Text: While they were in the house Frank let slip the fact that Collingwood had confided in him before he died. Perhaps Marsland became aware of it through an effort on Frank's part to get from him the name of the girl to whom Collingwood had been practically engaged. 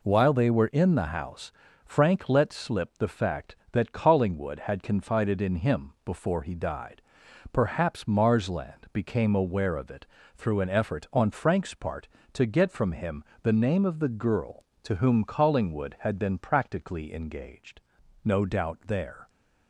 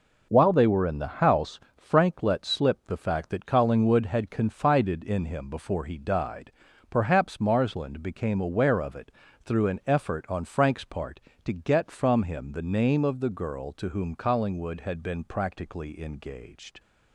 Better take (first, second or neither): second